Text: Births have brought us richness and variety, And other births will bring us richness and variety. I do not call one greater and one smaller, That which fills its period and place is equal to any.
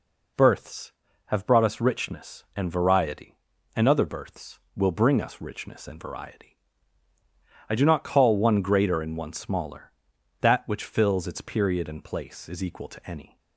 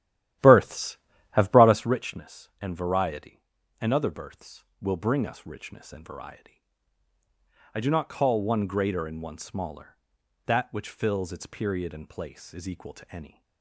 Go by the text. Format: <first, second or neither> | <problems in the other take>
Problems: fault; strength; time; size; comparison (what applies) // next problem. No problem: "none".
first | starts louder than the rest; strong; until 2.0 s; 12.5 dB